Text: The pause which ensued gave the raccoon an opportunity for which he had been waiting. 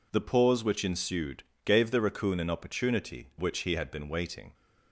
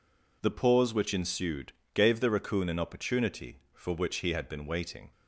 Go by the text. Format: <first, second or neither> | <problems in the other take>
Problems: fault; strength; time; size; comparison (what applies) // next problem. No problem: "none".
second | pauses between "ensued" and "gave"; slight; at 1.4 s; 0.22 s long; slight in the second // skips "for"; at 3.3 s